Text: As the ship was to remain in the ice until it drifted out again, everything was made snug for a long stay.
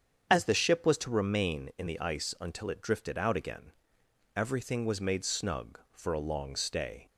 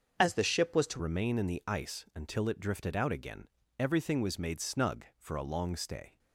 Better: first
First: starts louder than the rest; strong; until 1.3 s; 8 dB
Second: starts louder than the rest; until 1.1 s; 6.5 dB // changes voice at "remain"; from 0.9 s on; 5.2 s long

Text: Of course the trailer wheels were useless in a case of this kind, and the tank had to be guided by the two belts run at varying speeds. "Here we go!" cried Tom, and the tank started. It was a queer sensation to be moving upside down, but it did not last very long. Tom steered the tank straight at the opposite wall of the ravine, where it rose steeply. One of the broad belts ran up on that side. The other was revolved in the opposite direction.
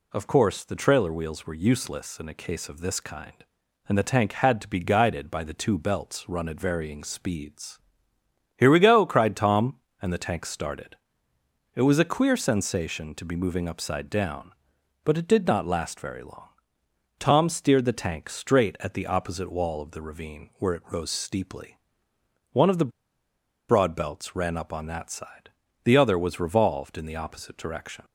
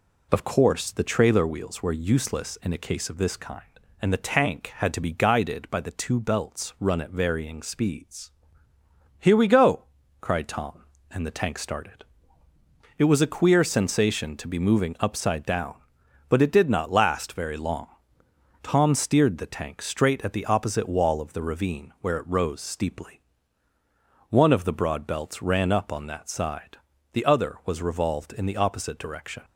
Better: second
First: pauses between "the" and "broad"; noticeable; at 22.9 s; 0.78 s long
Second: none

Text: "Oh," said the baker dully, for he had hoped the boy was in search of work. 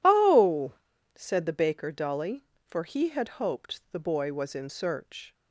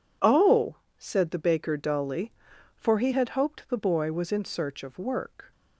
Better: second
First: stops before "of work"; at 5.3 s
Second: none

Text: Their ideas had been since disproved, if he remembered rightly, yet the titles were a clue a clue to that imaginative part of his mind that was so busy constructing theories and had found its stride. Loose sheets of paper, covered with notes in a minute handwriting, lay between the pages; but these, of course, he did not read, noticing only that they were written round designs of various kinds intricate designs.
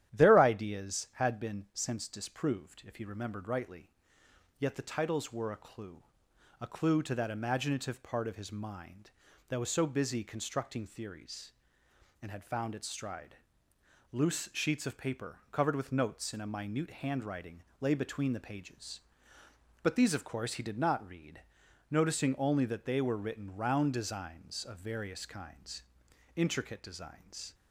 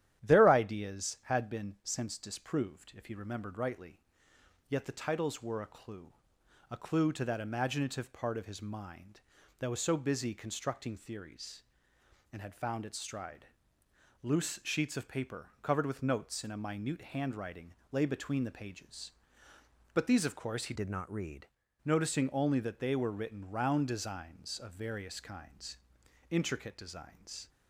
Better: first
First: starts louder than the rest; strong; until 1.1 s; 11.5 dB // pauses between "clue" and "a"; noticeable; at 6.0 s; 0.58 s long // pauses between "kinds" and "intricate"; noticeable; at 25.8 s; 0.52 s long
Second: starts louder than the rest; strong; until 1.2 s; 11.5 dB // pauses between "clue" and "a"; noticeable; at 6.1 s; 0.58 s long // changes voice from "did" to "read"; from 20.7 to 21.4 s; 0.7 s long // pauses between "kinds" and "intricate"; noticeable; at 25.7 s; 0.52 s long

